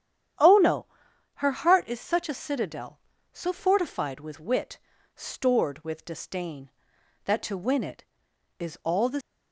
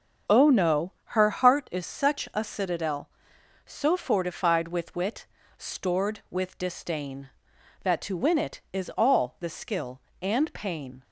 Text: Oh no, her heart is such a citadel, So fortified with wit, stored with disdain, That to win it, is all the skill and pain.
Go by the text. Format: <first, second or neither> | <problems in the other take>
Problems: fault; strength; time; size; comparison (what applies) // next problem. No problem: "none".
second | starts louder than the rest; strong; until 1.8 s; 9.5 dB; strong in the second // stops before "skill and pain"; at 9.2 s